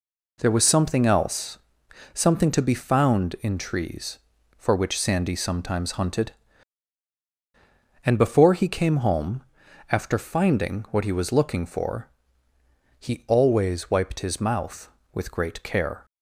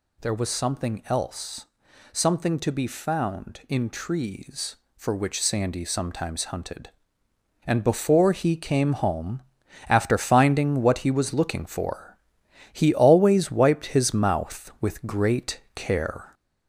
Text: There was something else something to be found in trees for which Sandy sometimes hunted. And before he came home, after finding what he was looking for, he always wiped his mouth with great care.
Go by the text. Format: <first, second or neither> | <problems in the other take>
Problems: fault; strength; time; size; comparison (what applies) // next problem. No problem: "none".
first | gets louder; throughout; 3.5 dB // pauses between "else" and "something"; noticeable; at 1.6 s; 0.46 s long; noticeable in the first // pauses between "great" and "care"; slight; at 15.5 s; 0.16 s long